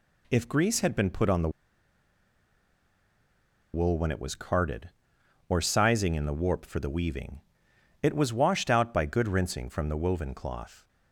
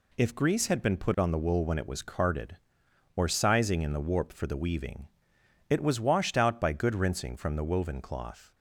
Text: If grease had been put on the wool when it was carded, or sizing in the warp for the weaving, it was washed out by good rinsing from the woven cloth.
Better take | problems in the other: second | pauses between "the" and "wool"; strong; at 1.4 s; 2.2 s long

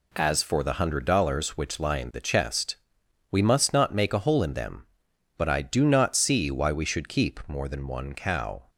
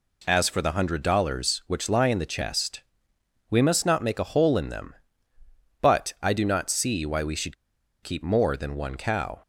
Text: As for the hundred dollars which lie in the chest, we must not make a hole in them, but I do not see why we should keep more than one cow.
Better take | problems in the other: first | pauses between "should" and "keep"; noticeable; at 7.5 s; 0.48 s long

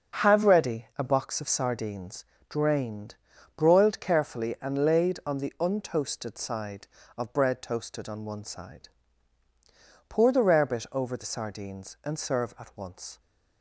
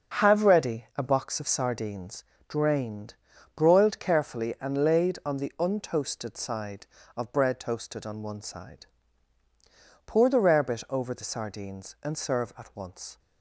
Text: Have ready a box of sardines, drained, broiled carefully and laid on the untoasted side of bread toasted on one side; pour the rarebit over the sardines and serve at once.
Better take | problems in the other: neither | none

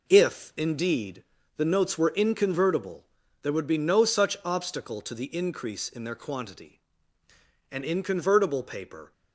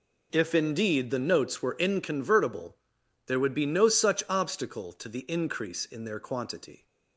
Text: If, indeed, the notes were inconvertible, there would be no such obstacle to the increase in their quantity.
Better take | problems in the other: second | goes on to say "An inconvertible paper"; from 7.6 s on; 1.4 s long

